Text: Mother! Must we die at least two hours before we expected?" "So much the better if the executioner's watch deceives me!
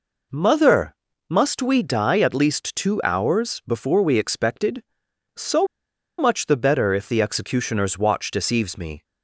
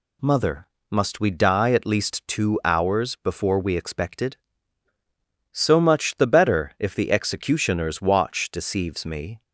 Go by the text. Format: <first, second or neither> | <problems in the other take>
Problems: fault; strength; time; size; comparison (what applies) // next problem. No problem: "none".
second | pauses between "So" and "much"; noticeable; at 5.6 s; 0.53 s long